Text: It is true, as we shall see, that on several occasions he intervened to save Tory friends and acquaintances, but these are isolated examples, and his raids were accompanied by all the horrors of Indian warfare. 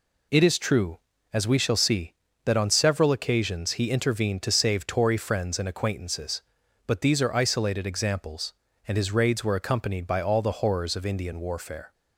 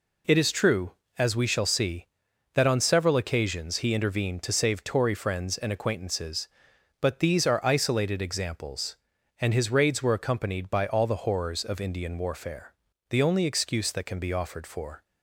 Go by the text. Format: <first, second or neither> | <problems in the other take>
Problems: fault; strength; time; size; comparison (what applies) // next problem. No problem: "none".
first | goes on to say "The only excuse that can be offered for"; strong; from 13.1 s on; 1.9 s long